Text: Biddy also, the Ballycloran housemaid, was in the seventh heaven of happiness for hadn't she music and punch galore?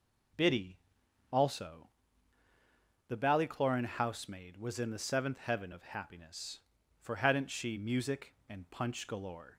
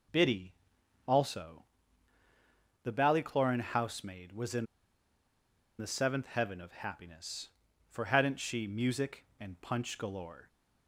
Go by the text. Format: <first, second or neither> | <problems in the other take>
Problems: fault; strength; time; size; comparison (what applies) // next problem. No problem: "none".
first | pauses between "Biddy" and "also"; noticeable; at 0.5 s; 0.54 s long; noticeable in the first // pauses between "in" and "the"; at 4.6 s; 1.1 s long